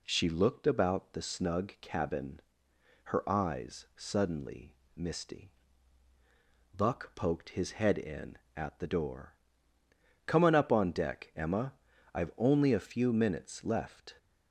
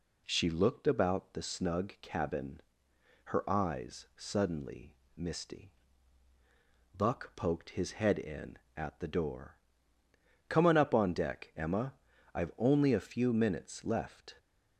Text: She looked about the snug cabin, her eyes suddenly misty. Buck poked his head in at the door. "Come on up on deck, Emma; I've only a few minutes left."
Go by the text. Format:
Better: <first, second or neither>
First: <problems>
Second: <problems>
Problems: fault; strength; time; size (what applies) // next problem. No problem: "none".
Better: neither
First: pauses between "suddenly" and "misty"; slight; at 4.7 s; 0.20 s long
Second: pauses between "suddenly" and "misty"; slight; at 4.9 s; 0.20 s long